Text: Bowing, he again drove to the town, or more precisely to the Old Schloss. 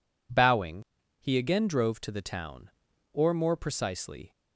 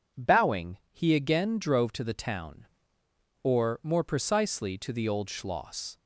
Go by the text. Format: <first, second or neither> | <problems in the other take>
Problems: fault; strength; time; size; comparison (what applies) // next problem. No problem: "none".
second | stops before "to the Old Schloss"; at 4.3 s